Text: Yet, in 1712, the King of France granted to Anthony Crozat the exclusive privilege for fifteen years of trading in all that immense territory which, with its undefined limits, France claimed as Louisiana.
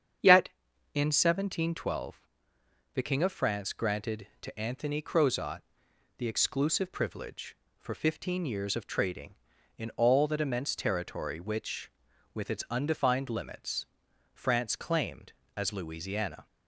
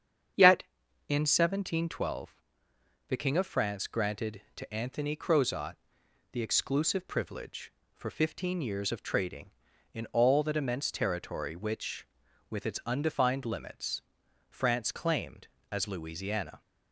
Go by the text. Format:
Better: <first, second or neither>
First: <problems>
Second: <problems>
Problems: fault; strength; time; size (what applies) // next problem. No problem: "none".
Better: neither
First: starts louder than the rest; strong; until 1.6 s; 8 dB // pauses between "Crozat" and "the"; noticeable; at 5.6 s; 0.56 s long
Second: starts louder than the rest; strong; until 1.7 s; 8 dB // pauses between "Crozat" and "the"; noticeable; at 5.7 s; 0.56 s long